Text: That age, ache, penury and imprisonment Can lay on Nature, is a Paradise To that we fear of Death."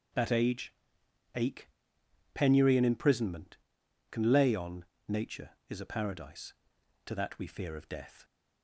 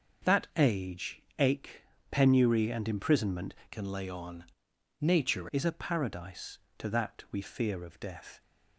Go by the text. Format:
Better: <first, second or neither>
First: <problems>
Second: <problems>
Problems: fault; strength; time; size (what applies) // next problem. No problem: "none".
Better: first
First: pauses between "on" and "Nature"; slight; at 4.8 s; 0.22 s long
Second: starts louder than the rest; until 1.4 s; 6.5 dB // changes voice from "Can" to "Nature"; from 3.7 to 5.4 s; 1.7 s long // pauses between "on" and "Nature"; noticeable; at 4.4 s; 0.56 s long